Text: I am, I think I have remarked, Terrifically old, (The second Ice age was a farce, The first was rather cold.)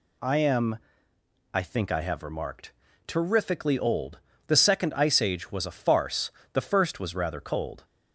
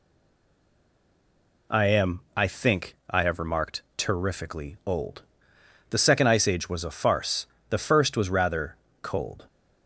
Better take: first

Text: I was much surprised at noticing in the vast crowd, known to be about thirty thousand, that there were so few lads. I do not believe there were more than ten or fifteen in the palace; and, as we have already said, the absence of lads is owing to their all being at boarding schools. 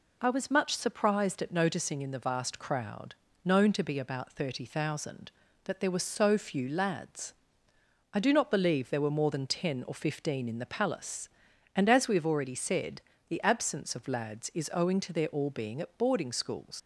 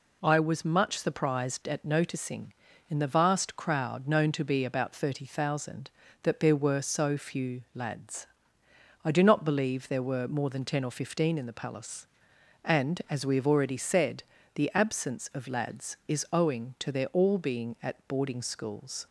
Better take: second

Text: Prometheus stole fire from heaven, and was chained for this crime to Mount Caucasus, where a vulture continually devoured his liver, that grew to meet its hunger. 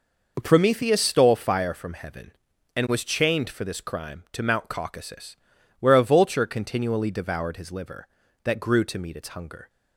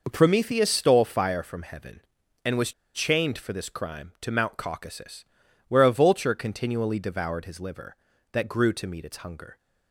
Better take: first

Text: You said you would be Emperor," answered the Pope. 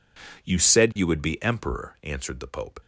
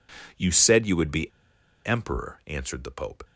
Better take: first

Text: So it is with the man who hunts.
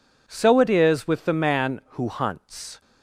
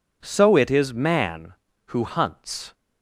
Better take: first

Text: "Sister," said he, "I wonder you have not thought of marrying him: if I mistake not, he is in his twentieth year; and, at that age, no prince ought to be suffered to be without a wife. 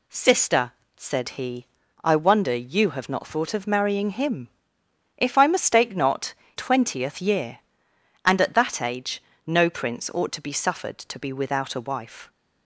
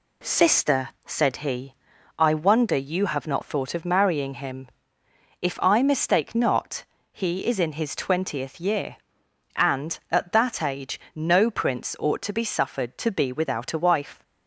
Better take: second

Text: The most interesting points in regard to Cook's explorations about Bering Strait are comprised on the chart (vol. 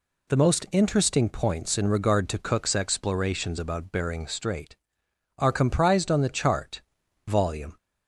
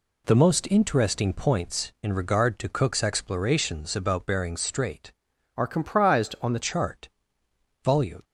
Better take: first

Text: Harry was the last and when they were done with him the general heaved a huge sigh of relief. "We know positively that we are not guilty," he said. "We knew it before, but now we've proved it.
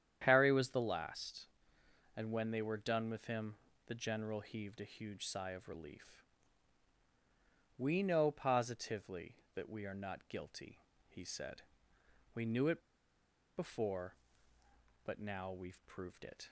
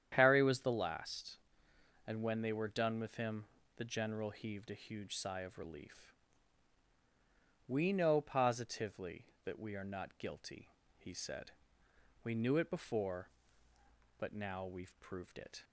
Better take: second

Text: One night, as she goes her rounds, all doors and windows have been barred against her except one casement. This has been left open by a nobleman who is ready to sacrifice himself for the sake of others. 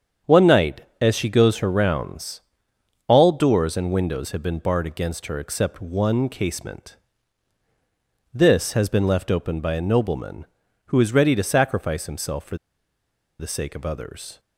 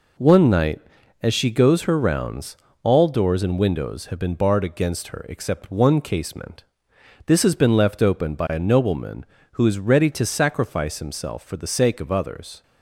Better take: second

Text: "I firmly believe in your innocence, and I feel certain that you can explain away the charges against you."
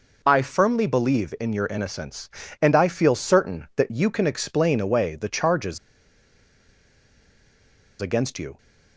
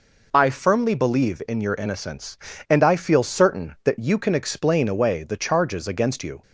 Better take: second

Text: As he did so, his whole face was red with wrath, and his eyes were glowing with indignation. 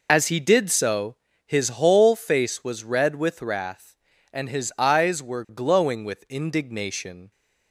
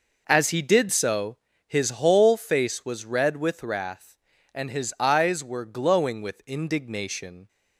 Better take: second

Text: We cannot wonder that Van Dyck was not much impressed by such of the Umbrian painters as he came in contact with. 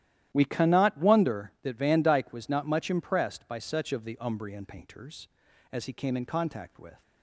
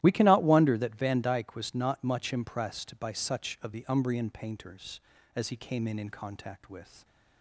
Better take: first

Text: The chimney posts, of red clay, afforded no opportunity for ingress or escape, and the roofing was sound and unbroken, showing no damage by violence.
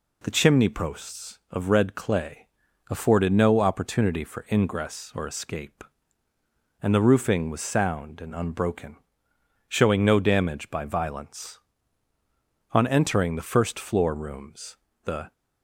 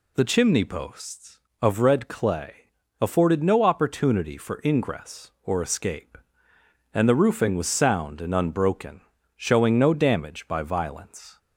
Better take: second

